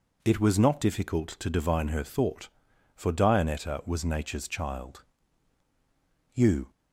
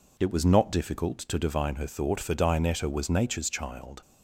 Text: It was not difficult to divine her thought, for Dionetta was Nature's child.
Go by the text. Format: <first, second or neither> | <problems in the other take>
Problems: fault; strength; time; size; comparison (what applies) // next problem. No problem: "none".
second | goes on to say "You"; slight; from 6.3 s on; 0.36 s long